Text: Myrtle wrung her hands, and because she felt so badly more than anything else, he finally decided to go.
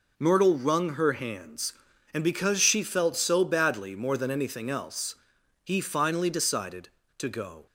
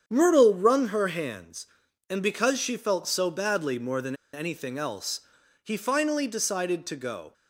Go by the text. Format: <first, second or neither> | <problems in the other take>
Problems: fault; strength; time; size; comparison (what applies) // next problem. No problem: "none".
first | starts louder than the rest; strong; until 1.0 s; 8 dB // pauses between "than" and "anything"; slight; at 4.1 s; 0.19 s long